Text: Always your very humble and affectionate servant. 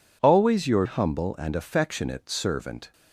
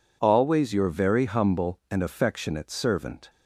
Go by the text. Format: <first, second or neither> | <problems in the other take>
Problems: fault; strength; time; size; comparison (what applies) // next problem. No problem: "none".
second | skips "very"; at 0.8 s